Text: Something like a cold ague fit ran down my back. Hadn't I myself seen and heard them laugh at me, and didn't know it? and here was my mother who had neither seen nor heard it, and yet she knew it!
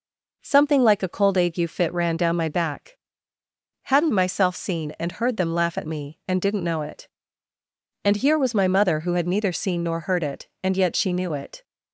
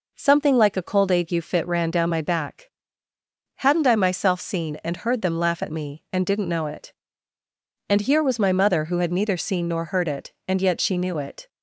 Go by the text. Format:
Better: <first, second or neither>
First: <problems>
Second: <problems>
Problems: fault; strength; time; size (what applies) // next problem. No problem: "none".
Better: second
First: skips "I"; at 4.1 s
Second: none